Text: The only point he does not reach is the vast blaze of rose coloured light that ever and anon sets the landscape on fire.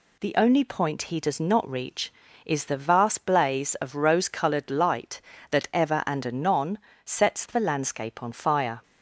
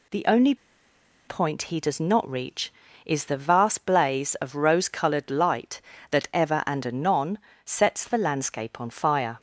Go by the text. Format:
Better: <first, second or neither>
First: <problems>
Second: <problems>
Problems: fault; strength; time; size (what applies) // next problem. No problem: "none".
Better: first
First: pauses between "anon" and "sets"; slight; at 6.7 s; 0.24 s long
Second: pauses between "only" and "point"; noticeable; at 0.5 s; 0.72 s long // pauses between "anon" and "sets"; slight; at 7.3 s; 0.24 s long